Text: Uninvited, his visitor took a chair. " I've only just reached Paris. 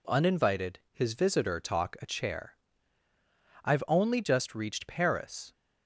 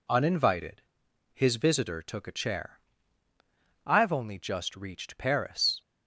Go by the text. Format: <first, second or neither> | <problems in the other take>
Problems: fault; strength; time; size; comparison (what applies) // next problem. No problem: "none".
second | says "talk" for "took"; at 1.5 s